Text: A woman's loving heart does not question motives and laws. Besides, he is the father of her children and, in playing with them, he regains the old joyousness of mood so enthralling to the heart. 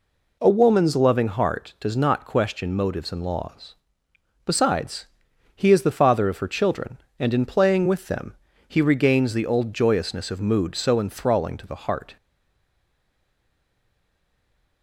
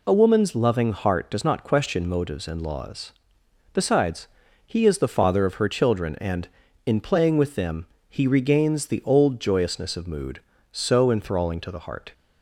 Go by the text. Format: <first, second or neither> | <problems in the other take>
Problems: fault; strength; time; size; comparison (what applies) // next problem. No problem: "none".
second | stays silent after the last word; strong; from 12.1 s on; 2.7 s long